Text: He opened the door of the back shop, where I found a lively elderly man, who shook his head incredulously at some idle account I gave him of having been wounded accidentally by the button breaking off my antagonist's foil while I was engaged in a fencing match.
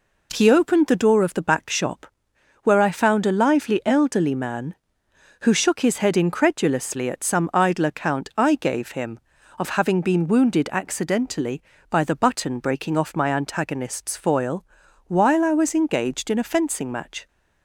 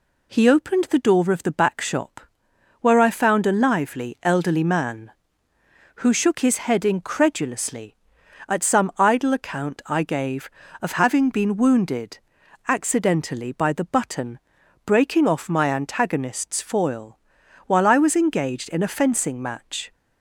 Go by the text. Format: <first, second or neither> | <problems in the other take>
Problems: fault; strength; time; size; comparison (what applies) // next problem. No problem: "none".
first | skips "him"; at 10.6 s // pauses between "wounded" and "accidentally"; noticeable; at 12.1 s; 0.48 s long // pauses between "button" and "breaking"; noticeable; at 14.3 s; 0.48 s long // pauses between "foil" and "while"; noticeable; at 17.1 s; 0.48 s long; also in the first